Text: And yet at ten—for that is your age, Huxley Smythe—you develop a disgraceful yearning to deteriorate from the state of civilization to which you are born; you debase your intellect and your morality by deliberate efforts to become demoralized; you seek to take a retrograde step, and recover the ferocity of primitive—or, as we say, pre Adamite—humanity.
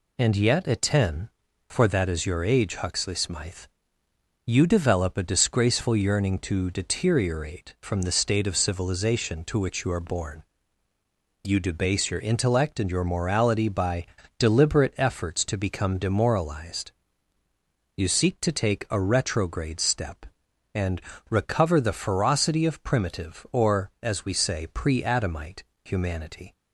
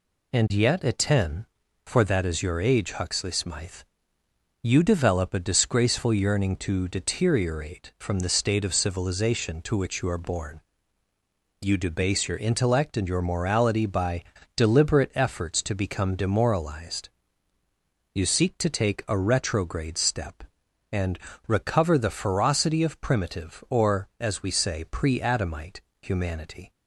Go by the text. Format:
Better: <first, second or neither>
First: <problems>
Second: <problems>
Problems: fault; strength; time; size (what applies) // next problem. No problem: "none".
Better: neither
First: pauses between "by" and "deliberate"; slight; at 14.0 s; 0.34 s long // pauses between "and" and "recover"; slight; at 21.0 s; 0.30 s long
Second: pauses between "by" and "deliberate"; slight; at 14.2 s; 0.34 s long // pauses between "and" and "recover"; slight; at 21.1 s; 0.30 s long